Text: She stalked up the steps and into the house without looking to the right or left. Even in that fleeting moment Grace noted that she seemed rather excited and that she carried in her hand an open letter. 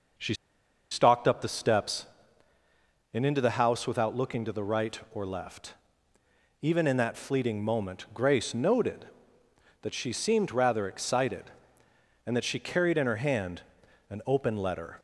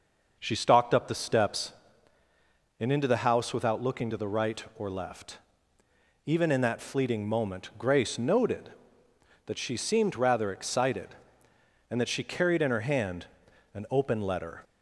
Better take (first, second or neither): second